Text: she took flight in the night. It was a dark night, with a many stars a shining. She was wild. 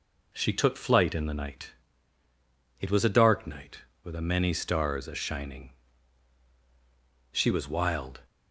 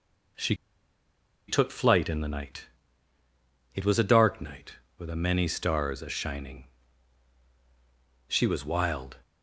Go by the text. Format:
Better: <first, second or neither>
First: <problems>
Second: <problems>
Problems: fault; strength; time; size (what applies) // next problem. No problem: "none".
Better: first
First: none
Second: pauses between "she" and "took"; noticeable; at 0.5 s; 0.94 s long